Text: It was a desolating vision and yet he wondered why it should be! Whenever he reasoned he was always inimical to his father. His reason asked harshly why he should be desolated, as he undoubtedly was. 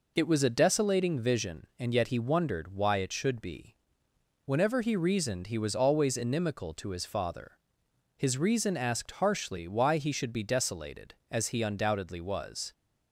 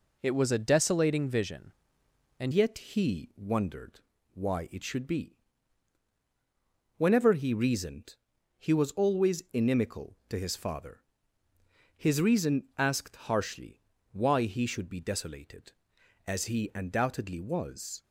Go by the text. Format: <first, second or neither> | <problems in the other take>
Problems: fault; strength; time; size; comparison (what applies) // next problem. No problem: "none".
first | changes voice at "yet"; from 2.5 s on; 15.5 s long // pauses between "wondered" and "why"; slight; at 4.0 s; 0.32 s long // pauses between "reasoned" and "he"; at 8.1 s; 0.42 s long // pauses between "harshly" and "why"; slight; at 13.8 s; 0.30 s long